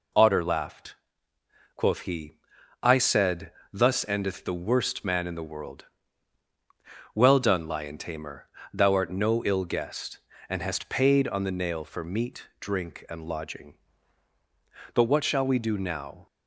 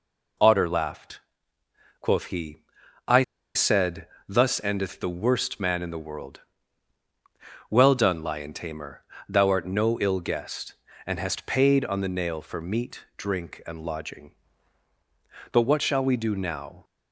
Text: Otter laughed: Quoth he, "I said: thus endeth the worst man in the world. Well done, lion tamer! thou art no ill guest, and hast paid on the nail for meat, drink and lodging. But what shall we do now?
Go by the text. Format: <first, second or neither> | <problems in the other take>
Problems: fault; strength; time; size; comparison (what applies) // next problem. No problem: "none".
first | pauses between "I" and "said"; slight; at 3.2 s; 0.31 s long